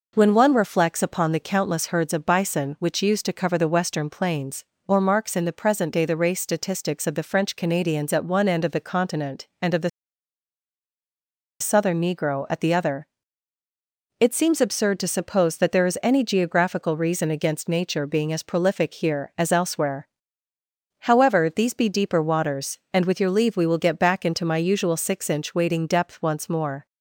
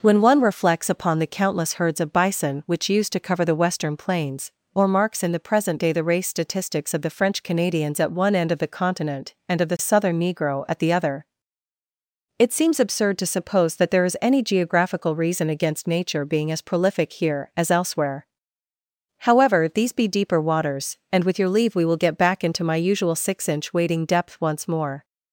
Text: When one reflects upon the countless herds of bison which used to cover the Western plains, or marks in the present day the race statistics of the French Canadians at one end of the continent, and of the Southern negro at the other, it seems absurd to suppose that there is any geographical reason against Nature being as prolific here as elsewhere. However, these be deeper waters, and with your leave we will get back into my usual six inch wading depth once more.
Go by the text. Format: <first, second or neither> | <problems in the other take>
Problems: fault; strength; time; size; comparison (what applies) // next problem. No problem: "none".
second | pauses between "the" and "Southern"; strong; at 9.8 s; 1.7 s long